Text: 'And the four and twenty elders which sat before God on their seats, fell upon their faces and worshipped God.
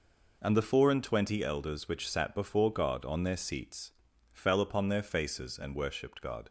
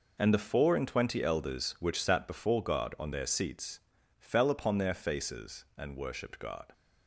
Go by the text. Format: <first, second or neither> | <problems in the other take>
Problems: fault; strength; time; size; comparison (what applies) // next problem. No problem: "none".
neither | none